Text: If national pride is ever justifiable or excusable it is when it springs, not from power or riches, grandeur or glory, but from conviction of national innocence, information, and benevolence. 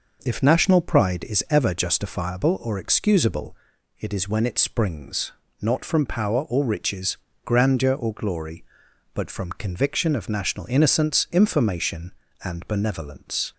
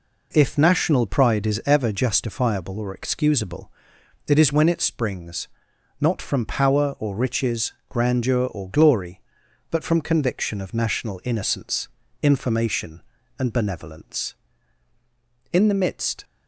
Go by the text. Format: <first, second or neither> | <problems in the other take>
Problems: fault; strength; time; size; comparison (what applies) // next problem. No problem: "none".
first | pauses between "excusable" and "it"; noticeable; at 3.6 s; 0.58 s long; also in the first // goes on to say "In the midst"; noticeable; from 15.5 s on; 0.72 s long